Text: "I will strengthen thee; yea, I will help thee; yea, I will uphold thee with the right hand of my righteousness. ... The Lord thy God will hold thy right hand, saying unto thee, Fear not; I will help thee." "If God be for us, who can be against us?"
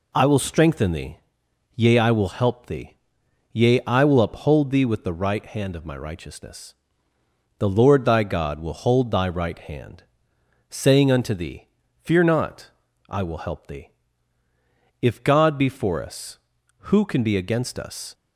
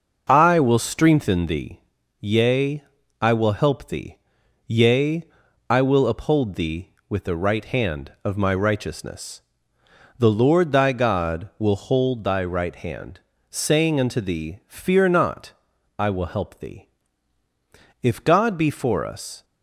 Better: first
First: none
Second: starts louder than the rest; noticeable; until 1.2 s; 6 dB // stops before "who can be against us"; at 19.4 s

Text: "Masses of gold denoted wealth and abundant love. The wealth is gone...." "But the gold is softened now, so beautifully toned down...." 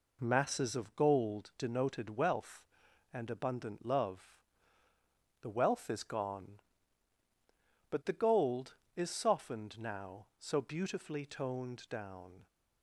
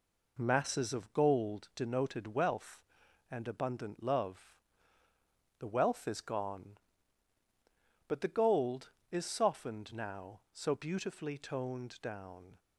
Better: neither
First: none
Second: none

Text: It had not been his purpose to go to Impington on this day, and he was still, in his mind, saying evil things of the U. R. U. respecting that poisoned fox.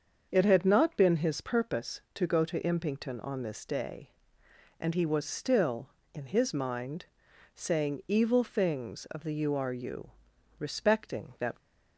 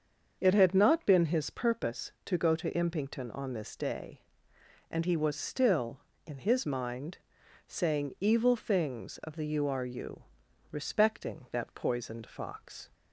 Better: second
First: starts louder than the rest; until 1.3 s; 6.5 dB // pauses between "U" and "respecting"; noticeable; at 10.1 s; 0.48 s long // stops before "poisoned fox"; at 11.5 s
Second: starts louder than the rest; until 1.4 s; 6.5 dB // pauses between "U" and "respecting"; noticeable; at 10.2 s; 0.48 s long

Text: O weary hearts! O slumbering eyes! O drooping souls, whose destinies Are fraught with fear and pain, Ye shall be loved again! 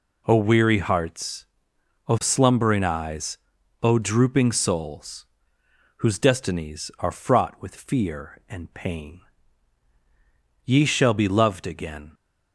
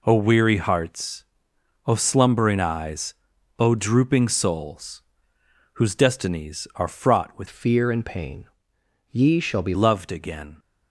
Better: first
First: none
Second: changes voice from "fear" to "be"; from 7.4 to 9.7 s; 2.3 s long

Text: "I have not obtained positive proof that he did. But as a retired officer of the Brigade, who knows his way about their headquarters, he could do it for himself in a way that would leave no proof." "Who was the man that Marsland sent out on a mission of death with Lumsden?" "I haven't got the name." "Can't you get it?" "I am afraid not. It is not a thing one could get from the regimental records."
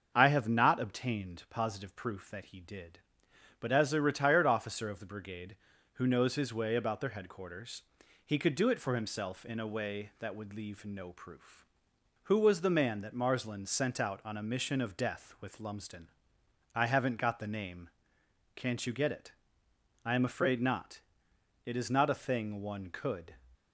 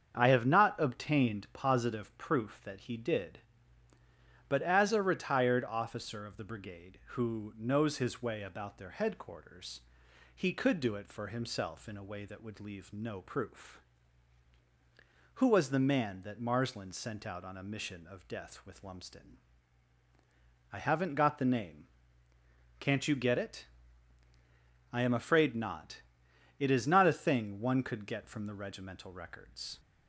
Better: second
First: starts louder than the rest; until 1.1 s; 6.5 dB // stops before "get from the regimental records"; at 23.5 s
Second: starts louder than the rest; strong; until 1.1 s; 7.5 dB

